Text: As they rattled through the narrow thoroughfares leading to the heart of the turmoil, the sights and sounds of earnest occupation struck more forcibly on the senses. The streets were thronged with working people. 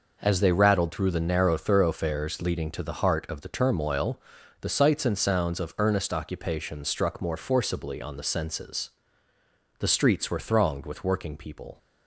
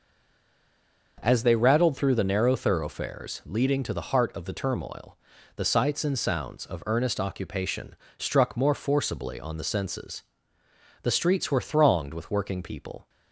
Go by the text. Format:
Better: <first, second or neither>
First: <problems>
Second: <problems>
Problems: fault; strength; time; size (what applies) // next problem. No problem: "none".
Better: first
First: none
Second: stays silent before the first word; until 1.1 s; 1.1 s long // starts louder than the rest; noticeable; until 2.2 s; 6 dB // pauses between "occupation" and "struck"; slight; at 7.9 s; 0.22 s long